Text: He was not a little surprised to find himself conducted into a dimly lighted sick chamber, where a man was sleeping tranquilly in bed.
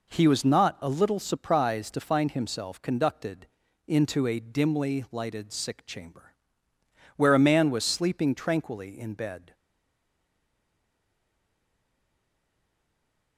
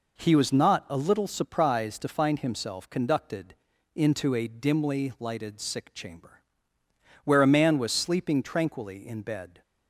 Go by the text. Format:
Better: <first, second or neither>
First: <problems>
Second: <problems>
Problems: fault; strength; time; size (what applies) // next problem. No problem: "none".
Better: second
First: pauses between "conducted" and "into"; at 3.4 s; 0.40 s long // stays silent after the last word; strong; from 9.5 s on; 3.8 s long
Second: pauses between "conducted" and "into"; at 3.5 s; 0.40 s long